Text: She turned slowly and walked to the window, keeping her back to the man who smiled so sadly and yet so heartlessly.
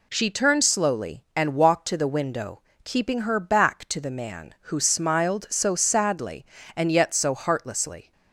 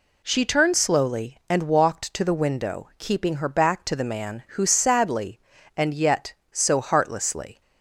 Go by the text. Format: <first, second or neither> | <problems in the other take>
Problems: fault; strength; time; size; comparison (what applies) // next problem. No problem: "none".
first | skips "smiled so"; at 4.6 s